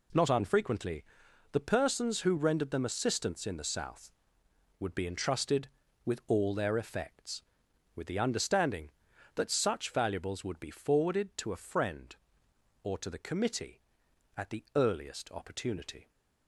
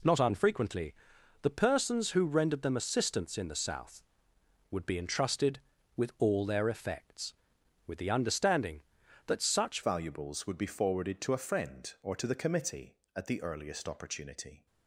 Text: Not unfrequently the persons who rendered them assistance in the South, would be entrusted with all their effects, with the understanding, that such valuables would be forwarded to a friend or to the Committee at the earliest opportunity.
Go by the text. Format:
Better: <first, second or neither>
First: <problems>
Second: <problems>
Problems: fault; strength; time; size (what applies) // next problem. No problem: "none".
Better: first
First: pauses between "unfrequently" and "the"; noticeable; at 1.0 s; 0.50 s long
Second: pauses between "unfrequently" and "the"; noticeable; at 0.9 s; 0.50 s long // changes voice at "valuables"; from 9.8 s on; 4.8 s long